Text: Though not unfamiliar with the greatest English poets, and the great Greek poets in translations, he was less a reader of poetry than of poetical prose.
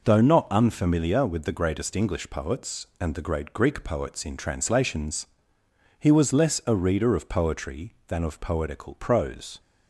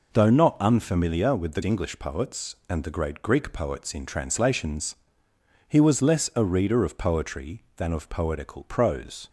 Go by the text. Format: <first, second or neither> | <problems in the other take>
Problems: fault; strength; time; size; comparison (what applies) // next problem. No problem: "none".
first | skips "greatest"; at 1.6 s